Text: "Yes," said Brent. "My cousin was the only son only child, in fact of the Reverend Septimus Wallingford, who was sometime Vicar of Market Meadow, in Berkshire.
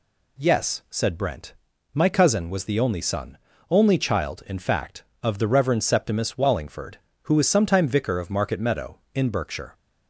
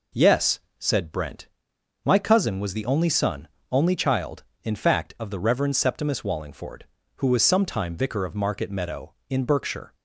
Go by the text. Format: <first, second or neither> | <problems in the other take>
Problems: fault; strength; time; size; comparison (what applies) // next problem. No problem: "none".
neither | pauses between "son" and "only"; slight; the same in both